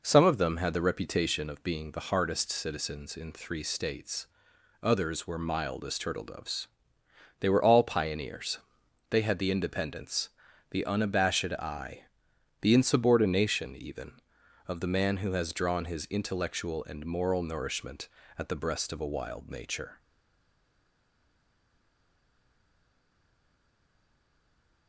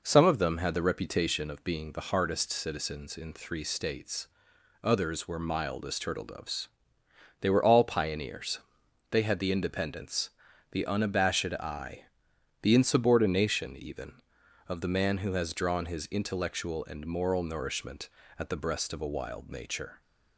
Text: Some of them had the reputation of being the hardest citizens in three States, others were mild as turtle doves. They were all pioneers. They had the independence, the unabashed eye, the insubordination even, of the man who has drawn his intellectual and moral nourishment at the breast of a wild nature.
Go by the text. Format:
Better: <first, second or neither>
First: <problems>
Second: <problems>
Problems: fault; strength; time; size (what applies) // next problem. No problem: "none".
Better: second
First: stays silent after the last word; strong; from 19.9 s on; 4.9 s long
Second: none